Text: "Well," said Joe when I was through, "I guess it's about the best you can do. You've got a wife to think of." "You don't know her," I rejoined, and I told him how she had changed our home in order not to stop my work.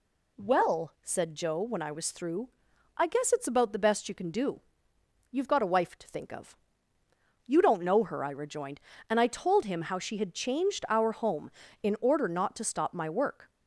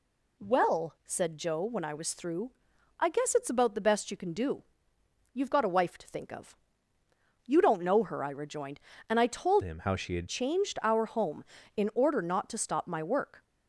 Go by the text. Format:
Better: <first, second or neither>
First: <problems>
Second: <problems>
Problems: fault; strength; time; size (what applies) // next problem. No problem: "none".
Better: first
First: none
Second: changes voice from "him" to "had"; from 9.6 to 10.2 s; 0.6 s long